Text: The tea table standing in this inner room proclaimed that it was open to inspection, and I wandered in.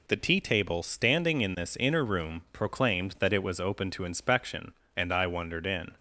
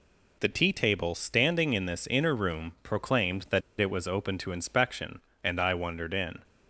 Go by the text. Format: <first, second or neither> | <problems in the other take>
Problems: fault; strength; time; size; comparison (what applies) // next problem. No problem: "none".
first | pauses between "that" and "it"; slight; at 3.6 s; 0.18 s long